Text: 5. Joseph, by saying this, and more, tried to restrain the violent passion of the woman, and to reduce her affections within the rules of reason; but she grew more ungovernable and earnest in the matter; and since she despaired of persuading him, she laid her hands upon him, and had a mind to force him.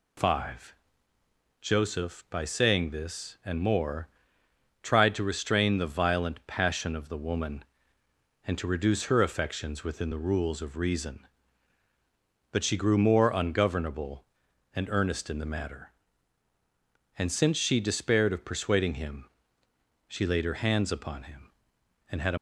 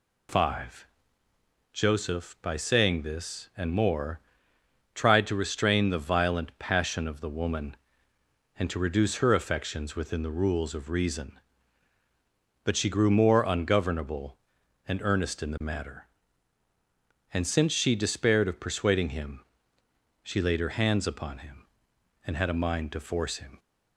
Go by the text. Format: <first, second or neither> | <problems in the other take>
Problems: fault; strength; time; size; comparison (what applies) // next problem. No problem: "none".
second | stops before "mind to force him"; at 22.3 s